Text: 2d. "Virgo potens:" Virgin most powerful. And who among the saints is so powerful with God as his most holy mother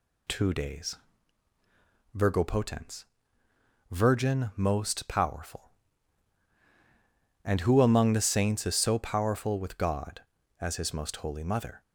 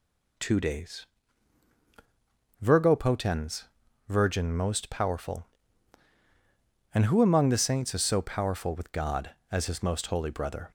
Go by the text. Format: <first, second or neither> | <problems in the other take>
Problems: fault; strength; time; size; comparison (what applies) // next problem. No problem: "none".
first | says "brother" for "mother"; at 10.3 s